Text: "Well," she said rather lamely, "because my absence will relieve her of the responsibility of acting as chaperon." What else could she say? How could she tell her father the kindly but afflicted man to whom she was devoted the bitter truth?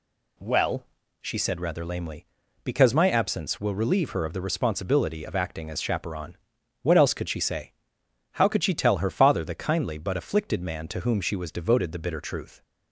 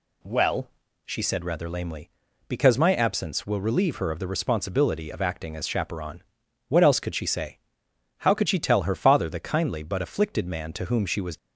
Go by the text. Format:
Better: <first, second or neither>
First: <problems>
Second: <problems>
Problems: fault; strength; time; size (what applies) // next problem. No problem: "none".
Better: first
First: none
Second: stops before "devoted the bitter truth"; at 11.3 s